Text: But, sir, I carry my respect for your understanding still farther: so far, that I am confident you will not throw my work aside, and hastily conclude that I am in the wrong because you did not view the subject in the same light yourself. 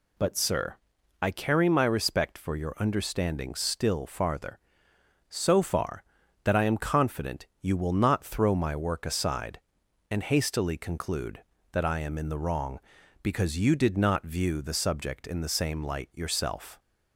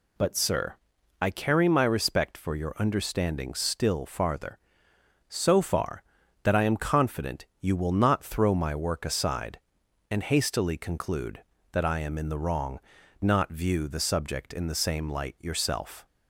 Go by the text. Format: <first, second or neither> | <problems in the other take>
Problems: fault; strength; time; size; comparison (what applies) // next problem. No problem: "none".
first | pauses between "confident" and "you"; slight; at 7.4 s; 0.16 s long; slight in the first // skips "because you did"; at 13.0 s